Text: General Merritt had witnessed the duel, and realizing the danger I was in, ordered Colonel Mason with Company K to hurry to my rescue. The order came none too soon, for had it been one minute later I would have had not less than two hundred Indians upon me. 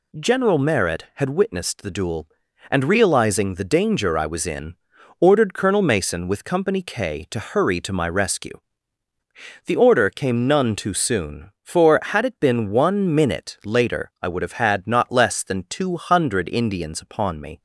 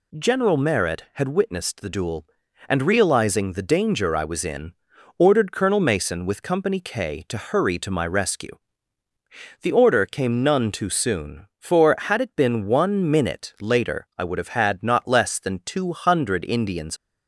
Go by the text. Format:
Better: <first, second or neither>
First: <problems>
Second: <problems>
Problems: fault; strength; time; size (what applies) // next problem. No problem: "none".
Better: first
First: none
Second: stops before "upon me"; at 16.9 s